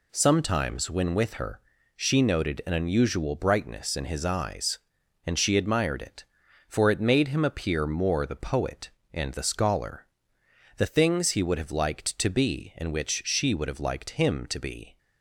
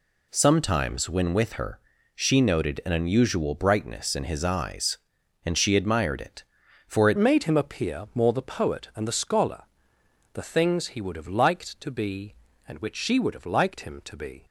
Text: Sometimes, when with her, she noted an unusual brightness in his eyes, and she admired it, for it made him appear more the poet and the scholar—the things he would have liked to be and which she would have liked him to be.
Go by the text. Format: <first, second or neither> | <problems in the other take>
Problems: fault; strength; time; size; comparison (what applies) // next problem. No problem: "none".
first | changes voice at "made"; from 7.1 s on; 7.3 s long